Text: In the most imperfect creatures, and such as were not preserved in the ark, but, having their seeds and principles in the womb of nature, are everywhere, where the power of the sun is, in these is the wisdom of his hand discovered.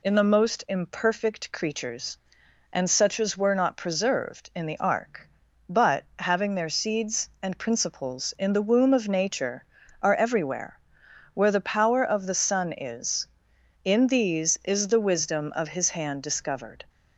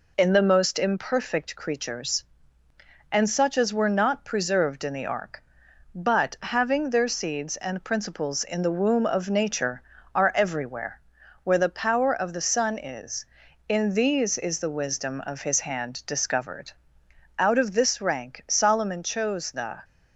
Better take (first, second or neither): first